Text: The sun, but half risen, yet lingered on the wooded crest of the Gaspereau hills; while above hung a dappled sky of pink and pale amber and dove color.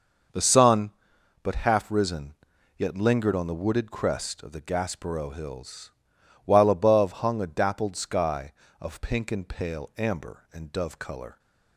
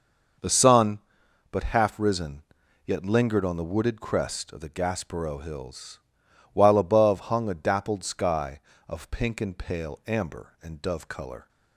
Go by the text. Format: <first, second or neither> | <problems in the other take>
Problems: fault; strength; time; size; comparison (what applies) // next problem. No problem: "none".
neither | none